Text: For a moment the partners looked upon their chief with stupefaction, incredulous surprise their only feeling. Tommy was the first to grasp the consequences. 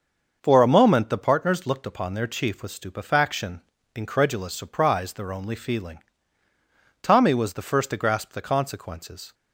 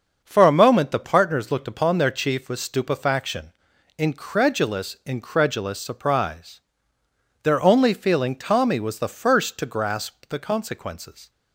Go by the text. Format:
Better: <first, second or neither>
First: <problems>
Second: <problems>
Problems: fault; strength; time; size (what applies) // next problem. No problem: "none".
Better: first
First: starts louder than the rest; until 1.4 s; 6.5 dB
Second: starts louder than the rest; until 1.2 s; 6.5 dB // says "incredulous" twice; at 5.0 s // pauses between "surprise" and "their"; noticeable; at 6.5 s; 0.84 s long